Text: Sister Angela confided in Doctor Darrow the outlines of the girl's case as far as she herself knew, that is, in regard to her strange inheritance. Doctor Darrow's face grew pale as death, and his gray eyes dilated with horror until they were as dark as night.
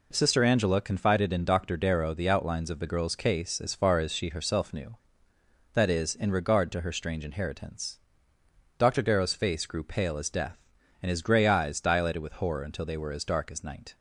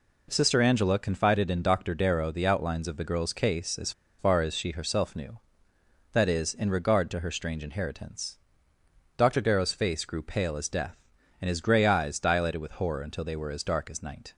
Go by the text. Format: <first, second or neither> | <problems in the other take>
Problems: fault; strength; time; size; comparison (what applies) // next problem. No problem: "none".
first | pauses between "as" and "far"; slight; at 3.9 s; 0.27 s long